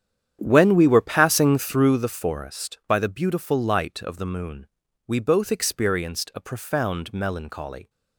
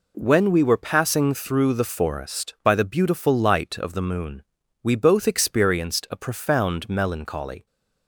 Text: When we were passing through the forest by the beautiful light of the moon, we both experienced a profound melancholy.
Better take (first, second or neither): second